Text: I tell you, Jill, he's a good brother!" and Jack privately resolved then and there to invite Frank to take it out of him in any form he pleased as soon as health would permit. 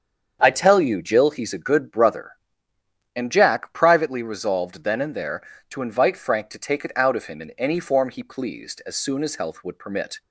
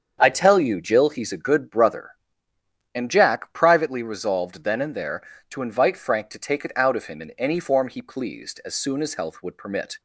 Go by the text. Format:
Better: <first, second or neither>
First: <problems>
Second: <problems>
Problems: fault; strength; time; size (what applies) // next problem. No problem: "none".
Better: neither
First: starts louder than the rest; strong; until 1.4 s; 7.5 dB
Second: starts louder than the rest; strong; until 1.2 s; 7.5 dB